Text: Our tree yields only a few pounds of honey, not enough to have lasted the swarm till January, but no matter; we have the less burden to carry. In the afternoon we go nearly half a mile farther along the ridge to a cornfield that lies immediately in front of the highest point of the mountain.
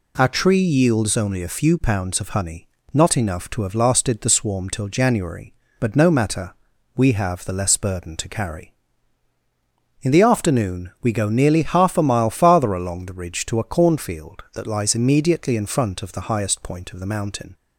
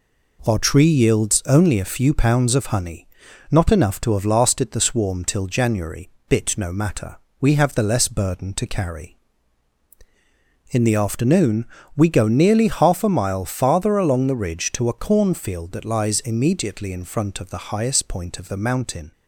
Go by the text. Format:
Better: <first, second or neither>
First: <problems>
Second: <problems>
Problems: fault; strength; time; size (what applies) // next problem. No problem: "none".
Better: first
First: none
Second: says "bit" for "but"; at 6.3 s // pauses between "afternoon" and "we"; slight; at 11.6 s; 0.28 s long